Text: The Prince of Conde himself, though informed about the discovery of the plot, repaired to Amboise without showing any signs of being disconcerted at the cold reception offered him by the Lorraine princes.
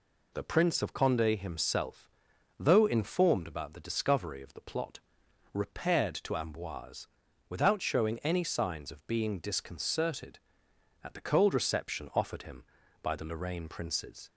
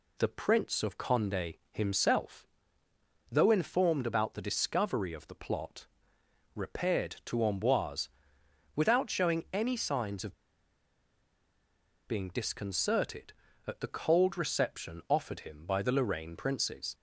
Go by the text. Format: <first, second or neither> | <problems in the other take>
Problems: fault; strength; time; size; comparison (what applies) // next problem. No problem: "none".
first | pauses between "Amboise" and "without"; noticeable; at 8.0 s; 0.66 s long; also in the first // pauses between "of" and "being"; strong; at 10.3 s; 1.7 s long